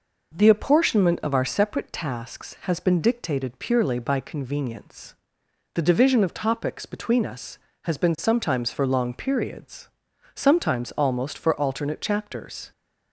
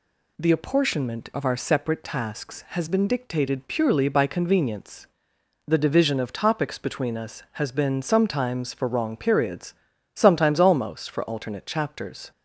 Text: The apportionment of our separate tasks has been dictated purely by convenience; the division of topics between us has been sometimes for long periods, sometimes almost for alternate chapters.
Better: first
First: none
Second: says "wrong" for "long"; at 8.8 s

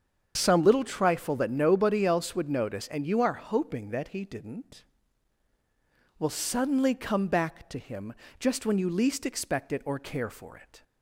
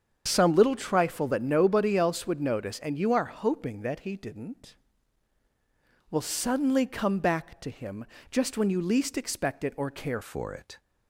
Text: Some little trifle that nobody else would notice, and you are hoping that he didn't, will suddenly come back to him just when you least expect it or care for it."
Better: first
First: starts louder than the rest; strong; until 1.3 s; 7.5 dB // pauses between "him" and "just"; slight; at 8.1 s; 0.26 s long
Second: starts louder than the rest; strong; until 1.2 s; 7.5 dB // pauses between "him" and "just"; slight; at 8.0 s; 0.26 s long // changes voice at "for"; from 10.2 s on; 0.5 s long

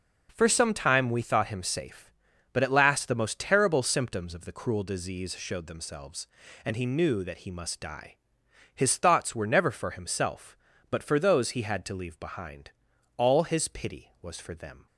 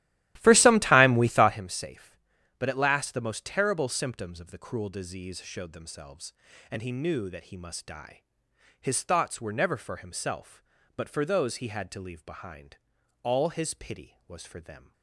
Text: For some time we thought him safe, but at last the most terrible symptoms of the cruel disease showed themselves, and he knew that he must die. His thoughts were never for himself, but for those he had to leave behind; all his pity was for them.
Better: first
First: none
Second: starts louder than the rest; strong; until 1.6 s; 14.5 dB

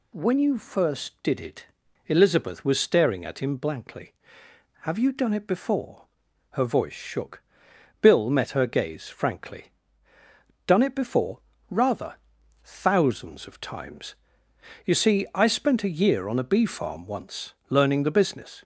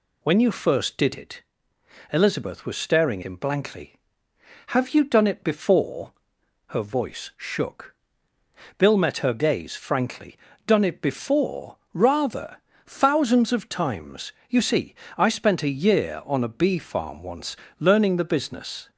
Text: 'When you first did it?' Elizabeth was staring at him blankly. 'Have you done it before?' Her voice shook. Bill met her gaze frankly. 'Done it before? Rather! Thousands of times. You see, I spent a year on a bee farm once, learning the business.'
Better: first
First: none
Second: skips "at"; at 3.2 s

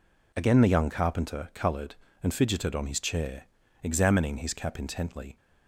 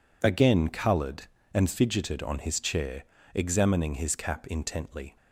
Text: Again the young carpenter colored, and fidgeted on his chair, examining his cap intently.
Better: first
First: none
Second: skips "the young carpenter"; at 0.6 s

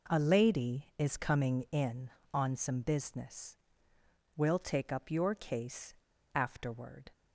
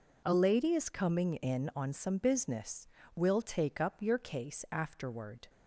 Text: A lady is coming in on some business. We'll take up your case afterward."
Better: second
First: pauses between "case" and "afterward"; at 5.9 s; 0.42 s long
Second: none

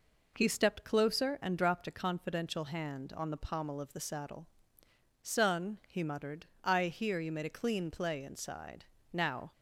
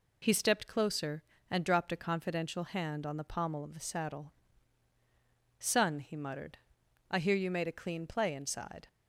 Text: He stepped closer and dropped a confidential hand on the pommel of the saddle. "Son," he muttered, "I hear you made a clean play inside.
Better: second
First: goes on to say "Now"; slight; from 9.1 s on; 0.40 s long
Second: none

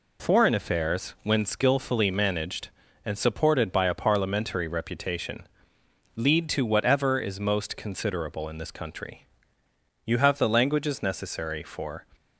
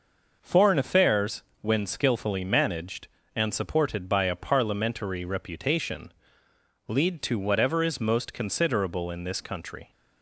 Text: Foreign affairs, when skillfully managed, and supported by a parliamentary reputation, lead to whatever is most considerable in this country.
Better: second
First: goes on to say "You have the languages necessary for"; strong; from 10.0 s on; 2.0 s long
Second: none

